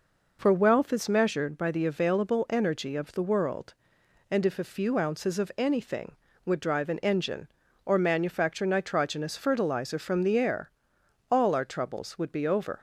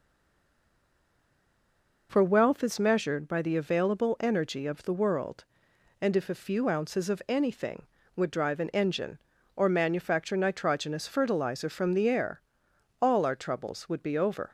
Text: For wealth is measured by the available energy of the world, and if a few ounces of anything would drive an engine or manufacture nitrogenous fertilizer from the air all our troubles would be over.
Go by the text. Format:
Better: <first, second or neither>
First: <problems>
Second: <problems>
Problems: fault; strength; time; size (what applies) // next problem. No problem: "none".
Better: first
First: pauses between "air" and "all"; noticeable; at 10.6 s; 0.60 s long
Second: stays silent before the first word; noticeable; until 2.0 s; 2.0 s long // pauses between "air" and "all"; noticeable; at 12.4 s; 0.60 s long